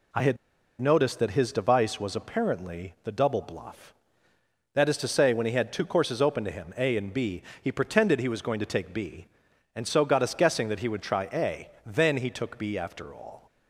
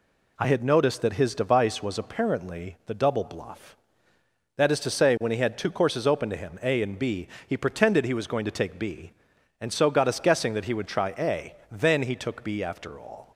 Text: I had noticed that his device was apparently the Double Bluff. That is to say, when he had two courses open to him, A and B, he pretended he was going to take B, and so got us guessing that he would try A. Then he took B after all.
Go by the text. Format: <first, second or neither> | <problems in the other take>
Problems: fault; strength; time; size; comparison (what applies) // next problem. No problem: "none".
second | pauses between "had" and "noticed"; at 0.3 s; 0.44 s long